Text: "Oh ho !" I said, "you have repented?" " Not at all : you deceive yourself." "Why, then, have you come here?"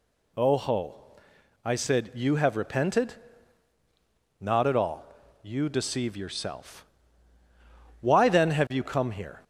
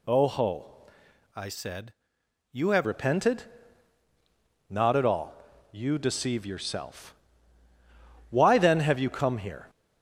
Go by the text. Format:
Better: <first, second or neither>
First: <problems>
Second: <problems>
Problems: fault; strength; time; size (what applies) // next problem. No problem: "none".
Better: first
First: none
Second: changes voice from "I" to "have"; from 1.3 to 2.8 s; 1.5 s long